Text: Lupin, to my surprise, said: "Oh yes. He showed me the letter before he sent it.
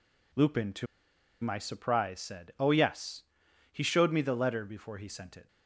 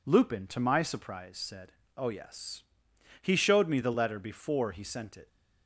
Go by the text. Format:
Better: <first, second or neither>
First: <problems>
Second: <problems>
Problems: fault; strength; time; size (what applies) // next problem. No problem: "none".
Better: second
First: pauses between "to" and "my"; noticeable; at 0.8 s; 0.55 s long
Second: none